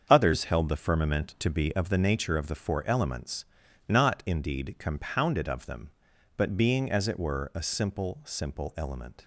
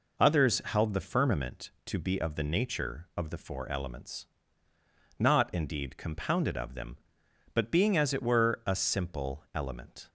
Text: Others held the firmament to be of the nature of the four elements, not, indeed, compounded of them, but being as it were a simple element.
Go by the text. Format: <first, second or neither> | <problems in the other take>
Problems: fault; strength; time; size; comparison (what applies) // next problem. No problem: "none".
second | starts louder than the rest; until 1.1 s; 7 dB // says "simple" twice; at 8.2 s